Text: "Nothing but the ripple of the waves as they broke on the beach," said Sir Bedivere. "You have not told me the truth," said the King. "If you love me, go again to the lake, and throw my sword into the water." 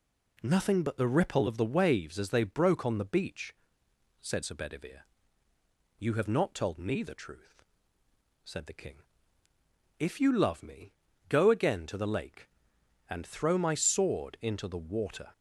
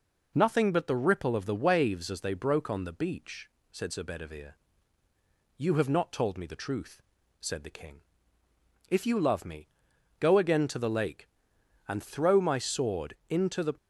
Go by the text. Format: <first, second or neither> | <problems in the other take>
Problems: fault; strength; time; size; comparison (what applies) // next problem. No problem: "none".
first | stops before "water"; at 13.7 s